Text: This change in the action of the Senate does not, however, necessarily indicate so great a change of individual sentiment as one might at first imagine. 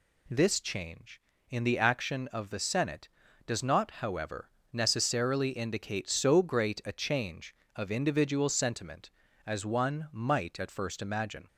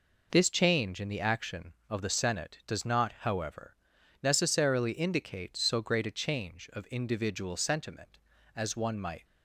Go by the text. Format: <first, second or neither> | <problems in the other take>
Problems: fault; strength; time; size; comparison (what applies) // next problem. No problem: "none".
first | stops before "at first imagine"; at 9.2 s